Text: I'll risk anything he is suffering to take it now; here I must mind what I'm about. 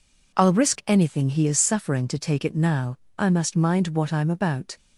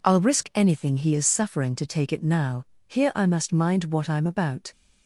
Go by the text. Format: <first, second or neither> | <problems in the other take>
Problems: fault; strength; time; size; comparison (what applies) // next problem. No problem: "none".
second | skips "here"; at 3.0 s